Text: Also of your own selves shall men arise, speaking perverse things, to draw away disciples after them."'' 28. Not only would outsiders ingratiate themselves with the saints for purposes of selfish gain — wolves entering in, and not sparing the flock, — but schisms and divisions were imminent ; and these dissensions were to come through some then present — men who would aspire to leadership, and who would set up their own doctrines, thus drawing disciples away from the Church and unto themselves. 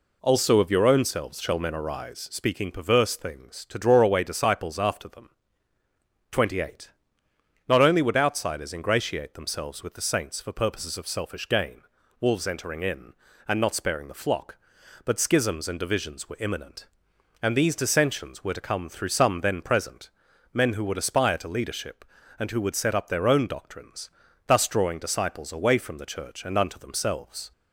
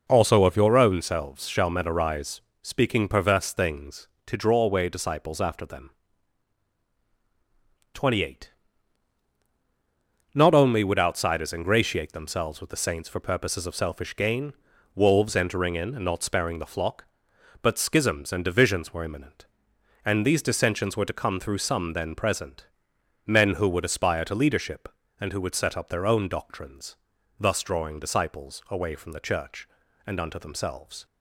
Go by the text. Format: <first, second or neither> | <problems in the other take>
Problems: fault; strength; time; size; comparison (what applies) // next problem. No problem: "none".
neither | none